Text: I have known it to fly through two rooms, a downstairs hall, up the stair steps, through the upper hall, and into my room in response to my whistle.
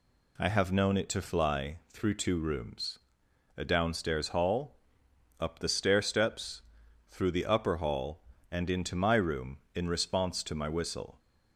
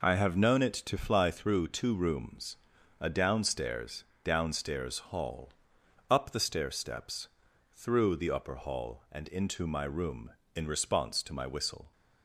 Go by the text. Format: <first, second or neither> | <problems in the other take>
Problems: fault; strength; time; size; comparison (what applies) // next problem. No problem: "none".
first | says "downstairs" twice; at 4.2 s